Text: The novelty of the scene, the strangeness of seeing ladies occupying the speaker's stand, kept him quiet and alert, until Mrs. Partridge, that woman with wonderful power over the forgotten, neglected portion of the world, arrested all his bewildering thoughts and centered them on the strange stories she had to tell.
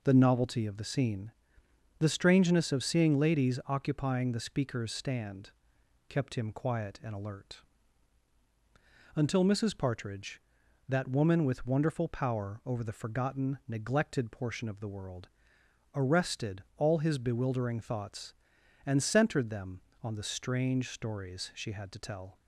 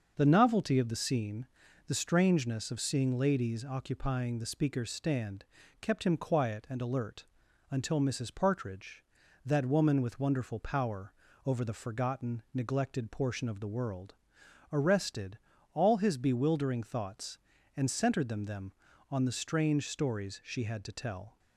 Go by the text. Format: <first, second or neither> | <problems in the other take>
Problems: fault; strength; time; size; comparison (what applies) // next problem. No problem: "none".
first | starts louder than the rest; until 1.1 s; 6.5 dB // pauses between "power" and "over"; slight; at 11.1 s; 0.34 s long // pauses between "arrested" and "all"; slight; at 15.3 s; 0.34 s long // says "them" twice; at 18.4 s